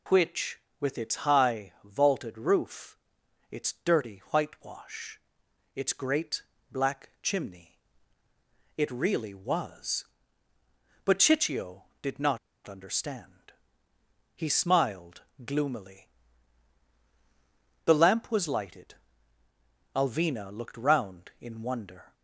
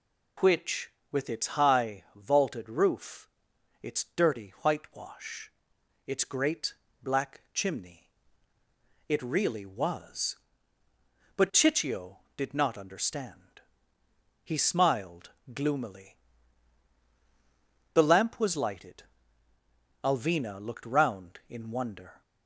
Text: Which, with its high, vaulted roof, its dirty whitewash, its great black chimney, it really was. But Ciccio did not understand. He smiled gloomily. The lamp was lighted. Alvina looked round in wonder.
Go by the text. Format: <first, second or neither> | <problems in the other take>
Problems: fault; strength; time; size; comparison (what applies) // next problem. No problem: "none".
second | pauses between "great" and "black"; slight; at 6.4 s; 0.28 s long; slight in the second // pauses between "not" and "understand"; slight; at 12.3 s; 0.28 s long // pauses between "smiled" and "gloomily"; slight; at 15.2 s; 0.24 s long; slight in the second